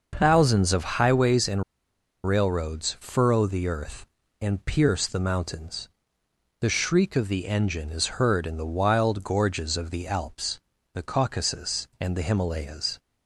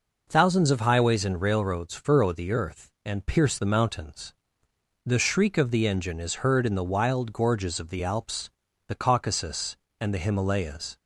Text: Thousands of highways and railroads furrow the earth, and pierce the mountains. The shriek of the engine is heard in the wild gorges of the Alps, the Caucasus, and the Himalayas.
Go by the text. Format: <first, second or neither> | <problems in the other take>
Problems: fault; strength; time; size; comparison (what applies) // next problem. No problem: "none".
second | pauses between "and" and "railroads"; noticeable; at 1.6 s; 0.63 s long